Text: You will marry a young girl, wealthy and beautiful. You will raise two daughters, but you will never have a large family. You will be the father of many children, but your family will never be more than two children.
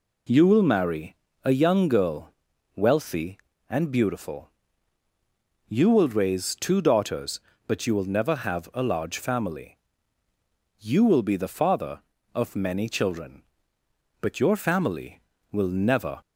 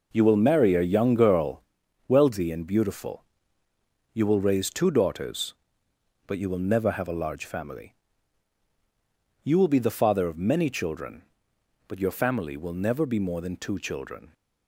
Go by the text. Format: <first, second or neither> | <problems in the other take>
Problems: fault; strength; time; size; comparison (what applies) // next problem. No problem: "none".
second | pauses between "marry" and "a"; slight; at 1.1 s; 0.30 s long // stops before "be more than two children"; at 16.2 s